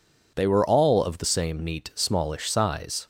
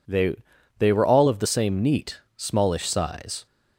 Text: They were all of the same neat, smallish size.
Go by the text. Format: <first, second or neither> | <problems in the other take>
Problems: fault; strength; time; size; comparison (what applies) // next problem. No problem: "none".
first | says "They" twice; at 0.7 s